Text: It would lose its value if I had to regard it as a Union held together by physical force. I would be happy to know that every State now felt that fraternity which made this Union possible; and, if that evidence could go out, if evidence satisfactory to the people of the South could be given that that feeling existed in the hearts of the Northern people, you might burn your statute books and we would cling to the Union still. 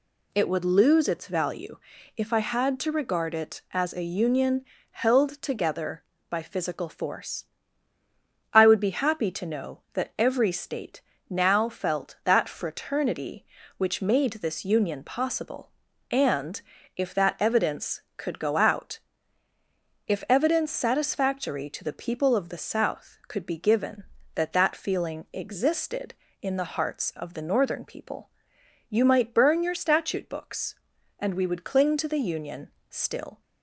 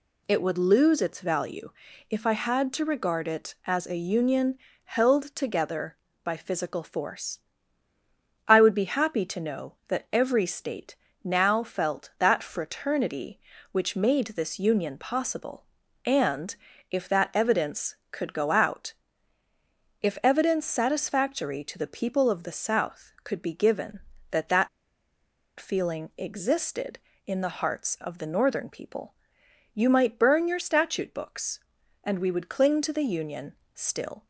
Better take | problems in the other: first | pauses between "value" and "if"; at 1.7 s; 0.38 s long; also in the first // pauses between "Union" and "held"; slight; at 4.5 s; 0.28 s long; slight in the first // pauses between "State" and "now"; slight; at 10.9 s; 0.30 s long; slight in the first // pauses between "that" and "feeling"; noticeable; at 24.6 s; 0.91 s long // pauses between "Union" and "still"; slight; at 33.5 s; 0.20 s long; slight in the first

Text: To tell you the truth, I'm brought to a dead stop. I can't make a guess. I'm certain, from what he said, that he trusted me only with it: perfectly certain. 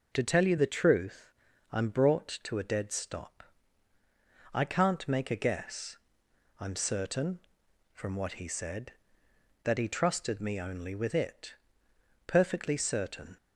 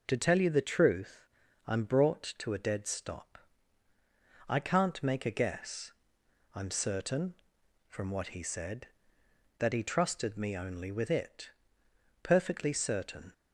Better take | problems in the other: neither | none

